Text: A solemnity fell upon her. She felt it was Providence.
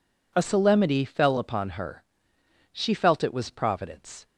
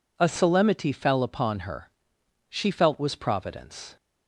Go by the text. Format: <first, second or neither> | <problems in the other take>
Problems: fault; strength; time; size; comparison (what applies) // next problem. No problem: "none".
first | skips "it"; at 2.9 s